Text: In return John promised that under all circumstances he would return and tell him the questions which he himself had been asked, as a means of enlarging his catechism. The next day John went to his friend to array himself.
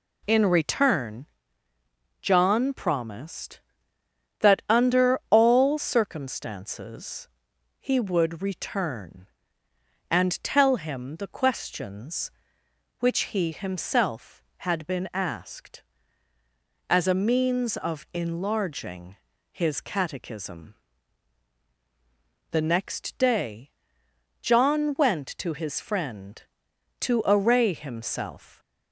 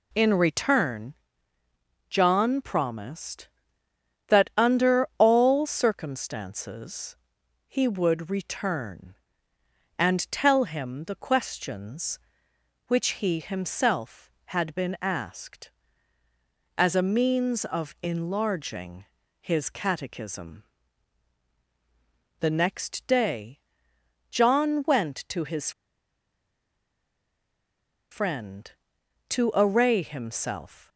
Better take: first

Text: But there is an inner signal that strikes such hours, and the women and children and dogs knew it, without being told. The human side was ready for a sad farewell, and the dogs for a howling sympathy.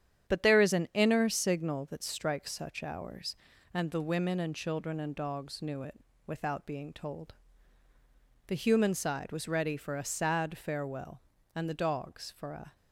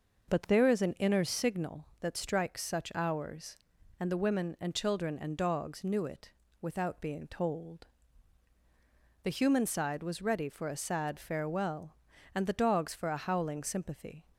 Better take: second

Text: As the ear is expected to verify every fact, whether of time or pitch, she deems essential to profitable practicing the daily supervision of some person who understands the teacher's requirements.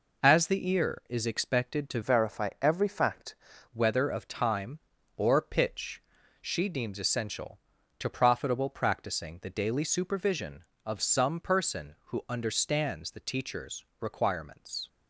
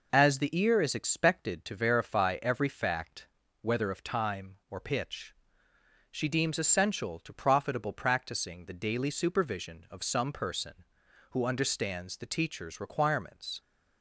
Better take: second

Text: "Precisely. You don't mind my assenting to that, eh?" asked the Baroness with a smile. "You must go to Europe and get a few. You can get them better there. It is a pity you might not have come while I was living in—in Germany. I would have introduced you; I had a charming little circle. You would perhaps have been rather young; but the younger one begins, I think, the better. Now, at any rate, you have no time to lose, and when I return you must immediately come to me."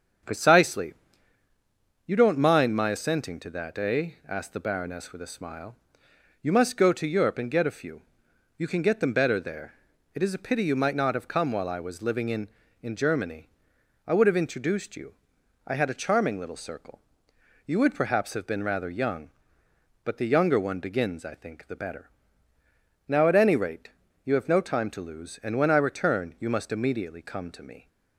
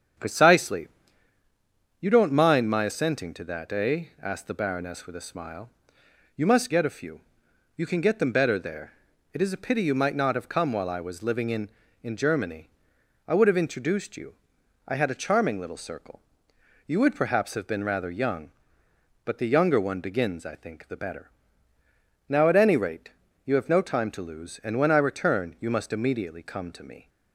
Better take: first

